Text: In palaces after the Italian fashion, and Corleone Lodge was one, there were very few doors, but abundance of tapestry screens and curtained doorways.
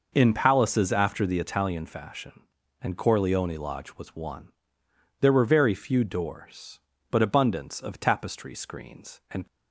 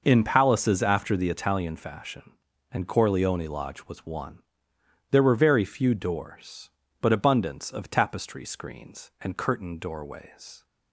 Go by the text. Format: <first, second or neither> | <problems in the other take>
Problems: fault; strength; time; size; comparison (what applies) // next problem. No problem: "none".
second | stops before "curtained doorways"; at 9.4 s